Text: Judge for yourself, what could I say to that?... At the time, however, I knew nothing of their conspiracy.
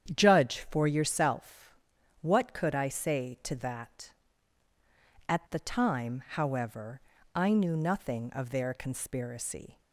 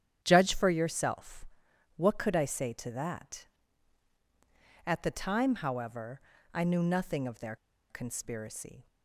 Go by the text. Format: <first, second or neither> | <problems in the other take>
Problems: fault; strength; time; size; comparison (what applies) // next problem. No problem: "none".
first | starts louder than the rest; strong; until 1.2 s; 9.5 dB; strong in the first // pauses between "their" and "conspiracy"; slight; at 7.5 s; 0.33 s long